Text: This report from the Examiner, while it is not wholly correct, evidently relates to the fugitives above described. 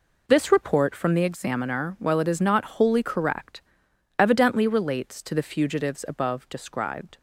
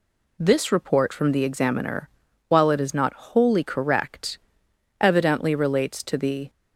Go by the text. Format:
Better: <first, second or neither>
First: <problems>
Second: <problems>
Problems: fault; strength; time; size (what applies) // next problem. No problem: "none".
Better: first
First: none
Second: stops before "fugitives above described"; at 6.4 s